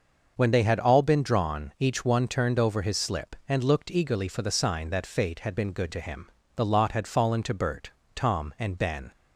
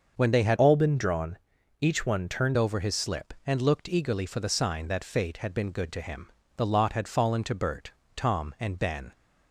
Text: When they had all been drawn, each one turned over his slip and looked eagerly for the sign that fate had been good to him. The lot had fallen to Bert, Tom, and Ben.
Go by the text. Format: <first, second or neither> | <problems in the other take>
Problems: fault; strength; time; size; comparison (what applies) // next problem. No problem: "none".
first | starts louder than the rest; until 1.1 s; 6.5 dB; also in the first // changes voice from "all" to "turned"; from 0.5 to 2.5 s; 2.0 s long